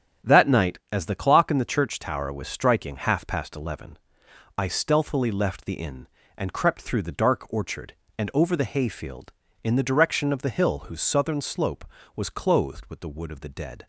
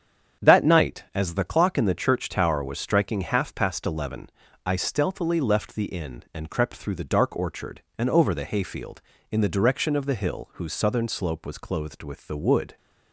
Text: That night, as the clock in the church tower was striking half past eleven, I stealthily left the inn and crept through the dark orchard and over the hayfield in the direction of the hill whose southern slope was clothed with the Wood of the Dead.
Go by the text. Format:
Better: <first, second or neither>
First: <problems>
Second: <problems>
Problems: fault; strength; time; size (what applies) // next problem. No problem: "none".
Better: first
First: starts louder than the rest; strong; until 1.3 s; 9 dB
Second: starts louder than the rest; strong; until 1.5 s; 8 dB // stops before "of the Dead"; at 12.7 s